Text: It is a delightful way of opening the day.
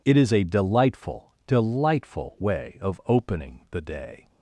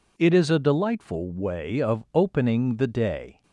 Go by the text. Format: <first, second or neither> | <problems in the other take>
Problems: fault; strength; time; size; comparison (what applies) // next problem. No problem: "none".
second | says "delightful" twice; at 1.4 s